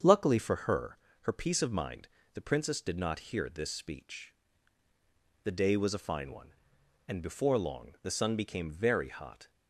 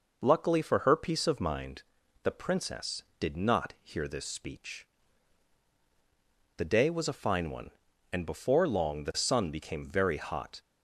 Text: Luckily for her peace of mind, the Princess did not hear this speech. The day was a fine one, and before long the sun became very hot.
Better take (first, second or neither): second